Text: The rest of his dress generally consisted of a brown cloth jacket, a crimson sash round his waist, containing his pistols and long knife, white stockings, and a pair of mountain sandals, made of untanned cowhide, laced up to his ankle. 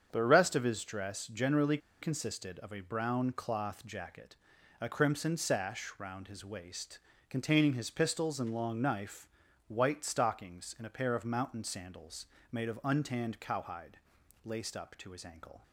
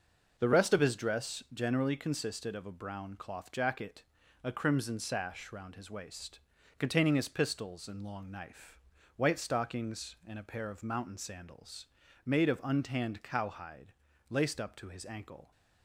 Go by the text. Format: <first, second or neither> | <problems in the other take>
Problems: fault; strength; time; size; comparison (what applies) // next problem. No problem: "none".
second | starts louder than the rest; strong; until 1.1 s; 7.5 dB // pauses between "generally" and "consisted"; slight; at 1.7 s; 0.24 s long